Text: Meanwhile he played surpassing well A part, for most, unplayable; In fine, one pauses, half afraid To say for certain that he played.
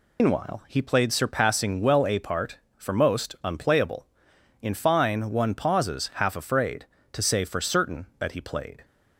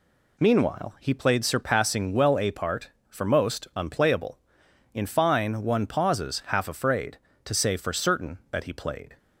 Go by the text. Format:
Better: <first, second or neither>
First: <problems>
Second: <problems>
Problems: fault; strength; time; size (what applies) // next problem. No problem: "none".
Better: second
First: loses the start of "Meanwhile"; at 0.1 s; 130 ms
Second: none